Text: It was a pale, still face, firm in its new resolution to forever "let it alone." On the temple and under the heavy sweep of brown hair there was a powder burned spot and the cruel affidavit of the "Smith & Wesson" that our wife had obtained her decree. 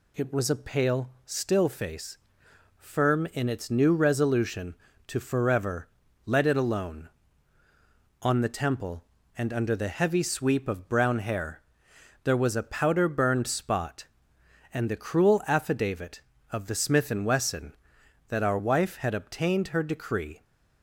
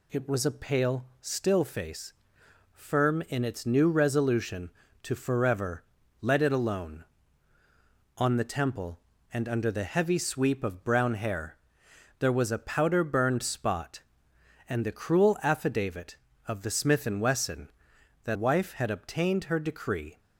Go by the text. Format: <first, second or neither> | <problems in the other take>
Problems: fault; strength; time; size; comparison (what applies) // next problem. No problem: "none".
first | pauses between "forever" and "let"; slight; at 5.8 s; 0.36 s long; slight in the first // pauses between "hair" and "there"; noticeable; at 11.5 s; 0.62 s long; noticeable in the first // skips "our"; at 18.3 s